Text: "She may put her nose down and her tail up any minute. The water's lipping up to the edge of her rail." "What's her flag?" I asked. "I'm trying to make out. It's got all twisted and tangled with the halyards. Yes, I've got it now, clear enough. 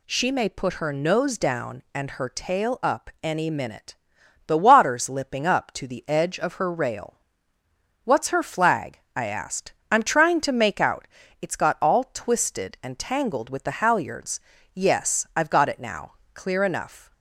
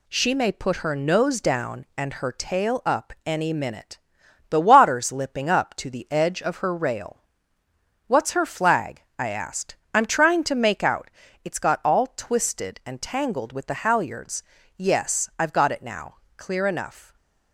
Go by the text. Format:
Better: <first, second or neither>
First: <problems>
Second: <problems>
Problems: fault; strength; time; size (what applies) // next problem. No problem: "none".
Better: first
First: none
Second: gets quieter; noticeable; throughout; 4.5 dB // stays silent after the last word; slight; from 17.0 s on; 0.5 s long